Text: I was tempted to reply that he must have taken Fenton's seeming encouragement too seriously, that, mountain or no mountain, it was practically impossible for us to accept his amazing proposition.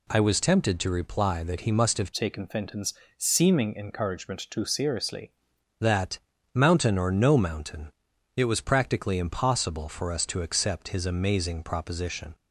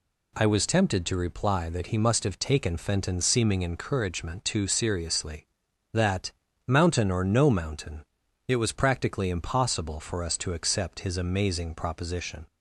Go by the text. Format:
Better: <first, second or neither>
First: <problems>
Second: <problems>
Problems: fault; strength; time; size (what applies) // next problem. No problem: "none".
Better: second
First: changes voice from "taken" to "seriously"; from 2.1 to 5.2 s; 3.1 s long // pauses between "Fenton's" and "seeming"; slight; at 2.9 s; 0.24 s long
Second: none